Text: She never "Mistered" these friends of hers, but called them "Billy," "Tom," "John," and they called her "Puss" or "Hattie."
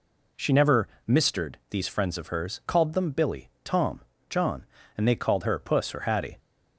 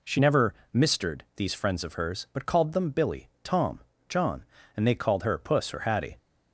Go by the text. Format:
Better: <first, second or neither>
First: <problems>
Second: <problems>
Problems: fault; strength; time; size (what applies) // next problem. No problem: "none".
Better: second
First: pauses between "never" and "Mistered"; slight; at 0.8 s; 0.18 s long // skips "but"; at 2.6 s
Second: pauses between "never" and "Mistered"; slight; at 0.5 s; 0.18 s long